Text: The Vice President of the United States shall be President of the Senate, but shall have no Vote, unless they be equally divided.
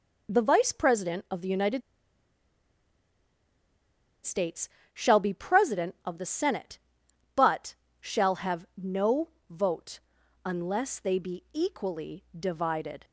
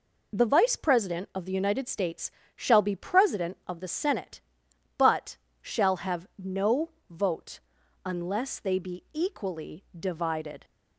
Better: second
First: pauses between "United" and "States"; strong; at 1.8 s; 2.4 s long // pauses between "States" and "shall"; slight; at 4.6 s; 0.24 s long // pauses between "but" and "shall"; slight; at 7.7 s; 0.26 s long // pauses between "have" and "no"; slight; at 8.6 s; 0.16 s long // pauses between "no" and "Vote"; slight; at 9.2 s; 0.22 s long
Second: pauses between "States" and "shall"; slight; at 2.3 s; 0.24 s long // pauses between "but" and "shall"; slight; at 5.3 s; 0.25 s long // pauses between "have" and "no"; slight; at 6.2 s; 0.16 s long // pauses between "no" and "Vote"; slight; at 6.8 s; 0.21 s long

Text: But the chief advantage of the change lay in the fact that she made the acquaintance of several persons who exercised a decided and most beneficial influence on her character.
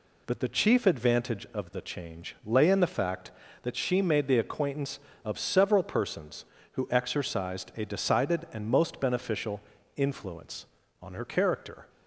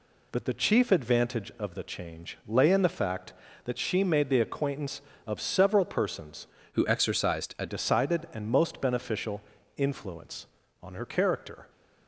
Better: first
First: pauses between "beneficial" and "influence"; slight; at 9.6 s; 0.36 s long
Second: changes voice from "who" to "a"; from 6.7 to 7.6 s; 0.9 s long // pauses between "beneficial" and "influence"; slight; at 9.4 s; 0.36 s long

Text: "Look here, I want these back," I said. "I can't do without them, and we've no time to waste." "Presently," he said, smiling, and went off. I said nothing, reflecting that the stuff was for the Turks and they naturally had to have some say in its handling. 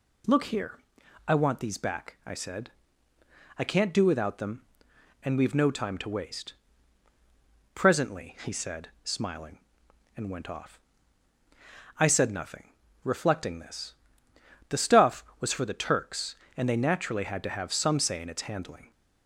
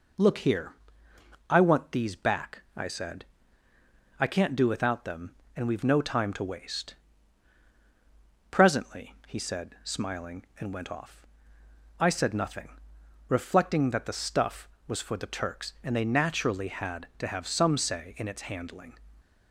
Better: second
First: says "this" for "that"; at 13.5 s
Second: none

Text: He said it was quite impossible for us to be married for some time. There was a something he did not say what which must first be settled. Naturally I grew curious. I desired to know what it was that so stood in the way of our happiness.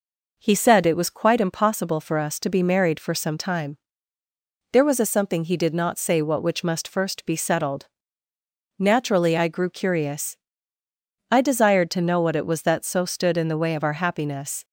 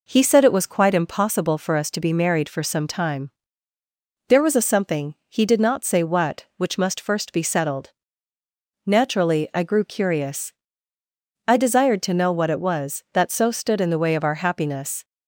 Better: neither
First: none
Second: none

